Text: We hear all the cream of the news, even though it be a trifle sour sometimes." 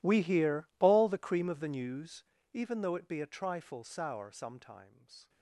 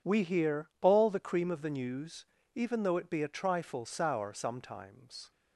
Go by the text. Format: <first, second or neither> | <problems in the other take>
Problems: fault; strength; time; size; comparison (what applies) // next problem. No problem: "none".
second | gets quieter; strong; throughout; 22.5 dB